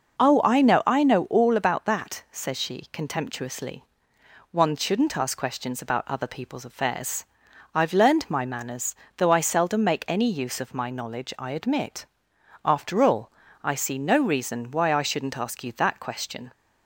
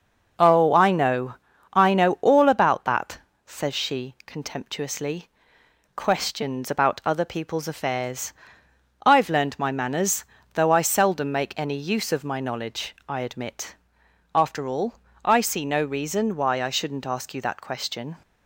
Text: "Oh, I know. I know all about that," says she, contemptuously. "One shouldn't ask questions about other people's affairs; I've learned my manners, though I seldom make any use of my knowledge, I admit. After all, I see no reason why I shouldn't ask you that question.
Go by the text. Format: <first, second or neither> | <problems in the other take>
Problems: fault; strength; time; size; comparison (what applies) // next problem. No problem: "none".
first | skips "One shouldn't ask"; at 5.6 s